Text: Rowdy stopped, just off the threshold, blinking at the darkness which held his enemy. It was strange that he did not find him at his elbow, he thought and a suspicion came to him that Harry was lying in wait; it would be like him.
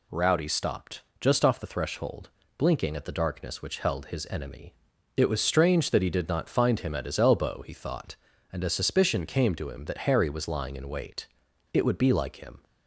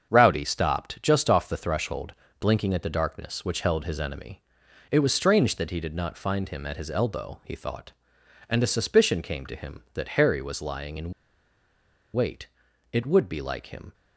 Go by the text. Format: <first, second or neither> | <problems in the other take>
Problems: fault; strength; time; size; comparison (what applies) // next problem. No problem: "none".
first | starts louder than the rest; until 1.1 s; 7 dB // pauses between "in" and "wait"; at 11.1 s; 1.0 s long